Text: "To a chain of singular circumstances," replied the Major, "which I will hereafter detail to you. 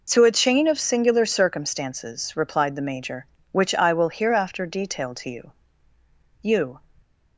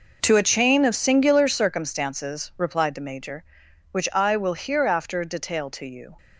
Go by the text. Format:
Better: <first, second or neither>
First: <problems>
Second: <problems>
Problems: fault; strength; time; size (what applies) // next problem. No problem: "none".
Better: second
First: says "you" twice; at 6.4 s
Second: none